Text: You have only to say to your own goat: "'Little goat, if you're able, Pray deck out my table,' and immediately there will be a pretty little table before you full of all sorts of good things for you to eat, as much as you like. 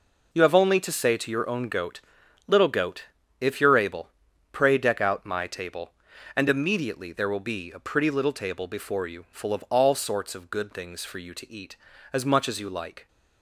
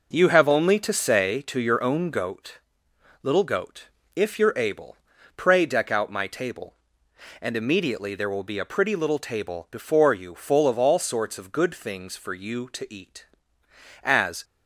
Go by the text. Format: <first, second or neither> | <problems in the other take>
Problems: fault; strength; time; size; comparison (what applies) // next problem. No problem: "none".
first | stops before "much as you like"; at 14.4 s